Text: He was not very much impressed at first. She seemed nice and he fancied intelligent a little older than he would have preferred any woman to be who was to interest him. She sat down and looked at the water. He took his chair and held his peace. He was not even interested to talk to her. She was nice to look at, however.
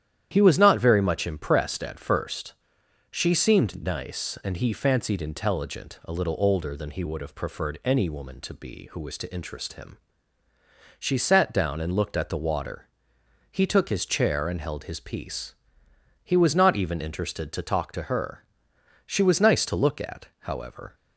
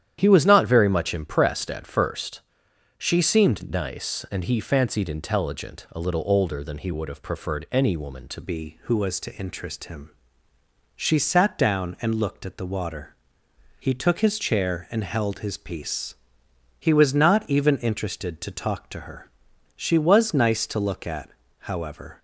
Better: first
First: starts louder than the rest; strong; until 1.3 s; 10.5 dB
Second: starts louder than the rest; strong; until 1.2 s; 10 dB // changes voice at "be"; from 8.4 s on; 13.7 s long

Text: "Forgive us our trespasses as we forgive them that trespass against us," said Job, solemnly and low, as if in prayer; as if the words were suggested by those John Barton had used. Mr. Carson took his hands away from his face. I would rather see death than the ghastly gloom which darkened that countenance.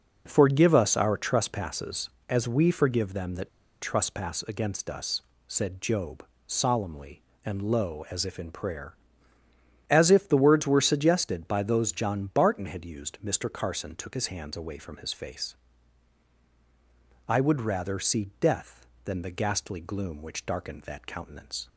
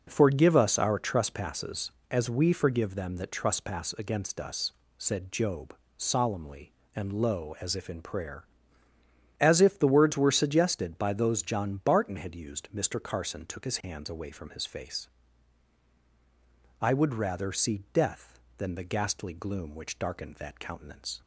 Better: second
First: pauses between "that" and "trespass"; slight; at 3.4 s; 0.32 s long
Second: none

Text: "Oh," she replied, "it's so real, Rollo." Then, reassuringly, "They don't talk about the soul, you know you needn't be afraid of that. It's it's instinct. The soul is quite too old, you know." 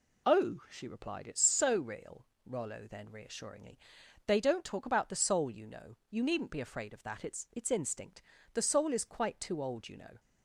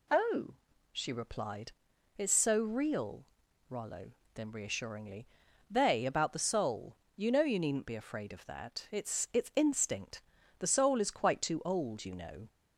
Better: first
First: none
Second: skips "don't talk"; at 6.0 s

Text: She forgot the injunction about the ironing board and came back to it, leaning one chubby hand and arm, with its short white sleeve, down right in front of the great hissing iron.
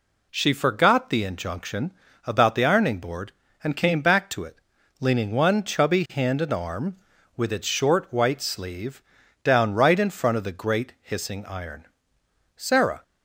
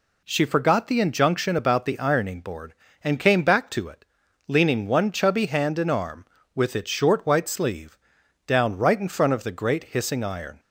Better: second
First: pauses between "injunction" and "about"; slight; at 1.9 s; 0.34 s long // goes on to say "Sarah"; slight; from 12.5 s on; 0.46 s long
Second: none

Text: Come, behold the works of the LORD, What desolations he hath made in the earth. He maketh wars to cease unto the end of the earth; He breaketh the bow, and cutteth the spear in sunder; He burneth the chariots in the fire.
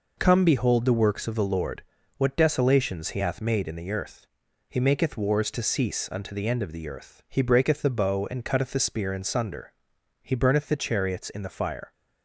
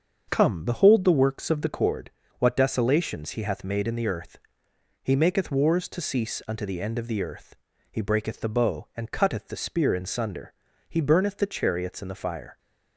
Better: first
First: none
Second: starts louder than the rest; strong; until 1.3 s; 7 dB // says "Cord" for "LORD"; at 1.6 s

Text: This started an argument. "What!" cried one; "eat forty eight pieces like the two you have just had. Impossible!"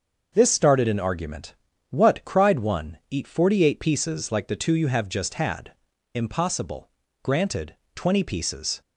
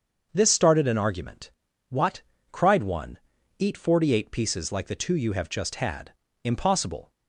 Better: second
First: starts louder than the rest; until 1.3 s; 6.5 dB // goes on to say "Granted twenty pieces"; from 7.2 s on; 1.5 s long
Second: starts louder than the rest; until 1.3 s; 6.5 dB

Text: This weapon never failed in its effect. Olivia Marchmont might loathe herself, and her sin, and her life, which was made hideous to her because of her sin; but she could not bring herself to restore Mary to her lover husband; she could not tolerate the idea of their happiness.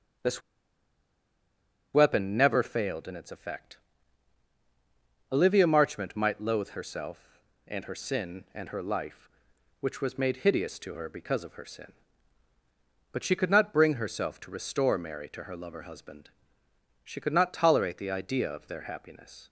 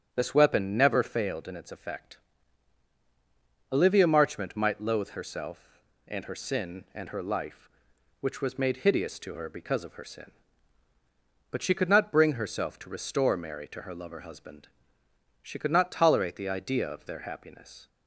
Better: second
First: starts louder than the rest; strong; until 2.7 s; 8.5 dB // pauses between "This" and "weapon"; strong; at 0.4 s; 1.5 s long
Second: starts louder than the rest; strong; until 1.1 s; 8.5 dB

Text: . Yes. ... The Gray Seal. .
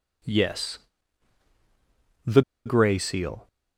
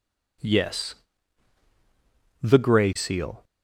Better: second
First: pauses between "The" and "Gray"; slight; at 2.4 s; 0.24 s long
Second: none

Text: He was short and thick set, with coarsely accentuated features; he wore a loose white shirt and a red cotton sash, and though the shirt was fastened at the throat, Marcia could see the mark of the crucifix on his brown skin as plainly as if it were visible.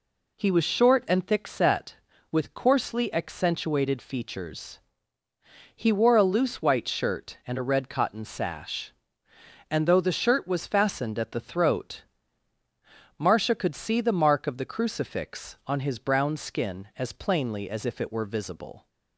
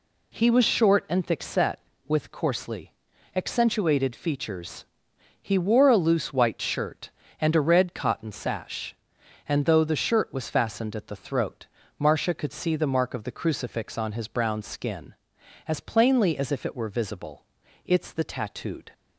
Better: first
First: none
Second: pauses between "coarsely" and "accentuated"; at 2.9 s; 0.40 s long // goes on to say "It's the tattooed"; noticeable; from 17.8 s on; 1.0 s long

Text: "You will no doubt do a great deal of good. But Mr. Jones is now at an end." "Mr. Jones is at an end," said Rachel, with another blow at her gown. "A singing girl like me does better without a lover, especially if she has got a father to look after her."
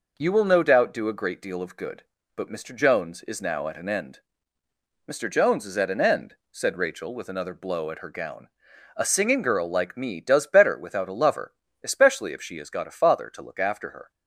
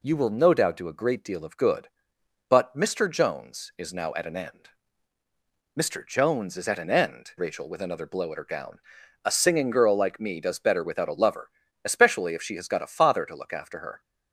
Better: first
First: none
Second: skips "said"; at 7.3 s

